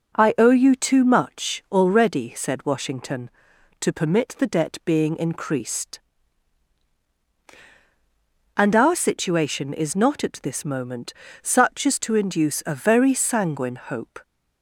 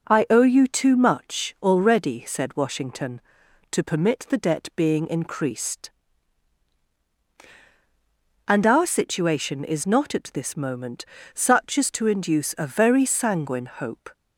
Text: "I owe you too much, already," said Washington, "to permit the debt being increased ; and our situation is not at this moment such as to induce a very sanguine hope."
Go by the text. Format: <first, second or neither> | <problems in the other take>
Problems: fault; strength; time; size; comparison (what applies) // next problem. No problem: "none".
neither | pauses between "moment" and "such"; slight; the same in both